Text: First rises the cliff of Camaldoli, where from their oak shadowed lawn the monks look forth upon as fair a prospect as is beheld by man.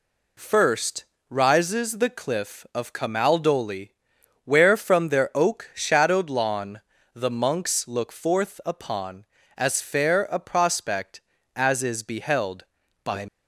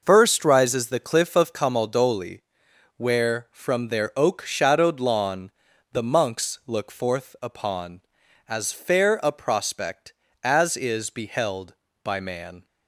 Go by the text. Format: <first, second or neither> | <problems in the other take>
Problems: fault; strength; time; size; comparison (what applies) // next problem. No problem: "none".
second | pauses between "First" and "rises"; slight; at 1.0 s; 0.26 s long // pauses between "lawn" and "the"; slight; at 6.8 s; 0.35 s long; also in the second // stops before "man"; at 13.2 s